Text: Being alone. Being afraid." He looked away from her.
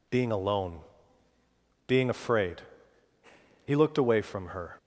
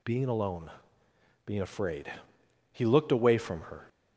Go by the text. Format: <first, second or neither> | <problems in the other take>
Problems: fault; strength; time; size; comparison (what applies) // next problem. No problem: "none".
neither | none